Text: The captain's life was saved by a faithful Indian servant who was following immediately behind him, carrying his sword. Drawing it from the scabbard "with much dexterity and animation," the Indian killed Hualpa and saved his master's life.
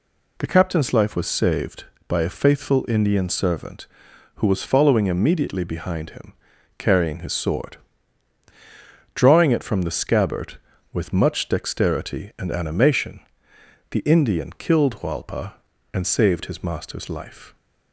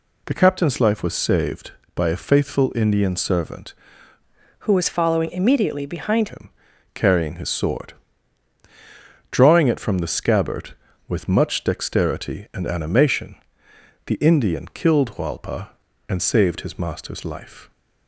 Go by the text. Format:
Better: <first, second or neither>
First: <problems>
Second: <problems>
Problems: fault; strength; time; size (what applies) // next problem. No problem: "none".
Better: first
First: none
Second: changes voice from "who" to "behind"; from 4.5 to 6.2 s; 1.7 s long